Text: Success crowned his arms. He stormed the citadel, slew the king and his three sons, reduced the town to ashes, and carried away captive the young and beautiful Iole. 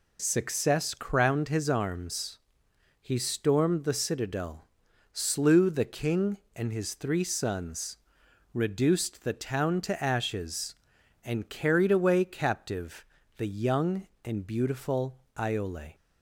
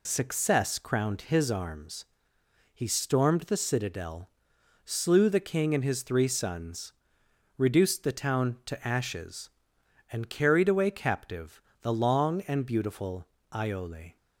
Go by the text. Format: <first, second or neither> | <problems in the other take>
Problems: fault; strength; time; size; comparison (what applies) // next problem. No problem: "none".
first | pauses between "captive" and "the"; slight; at 11.6 s; 0.22 s long; slight in the first // says "long" for "young"; at 11.9 s // pauses between "beautiful" and "Iole"; slight; at 13.2 s; 0.26 s long; slight in the first